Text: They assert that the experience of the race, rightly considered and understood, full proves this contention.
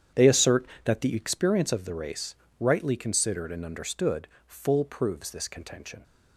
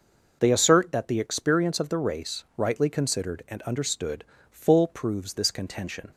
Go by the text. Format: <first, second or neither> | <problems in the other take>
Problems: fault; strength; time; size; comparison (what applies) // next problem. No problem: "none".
second | starts louder than the rest; strong; until 1.4 s; 9 dB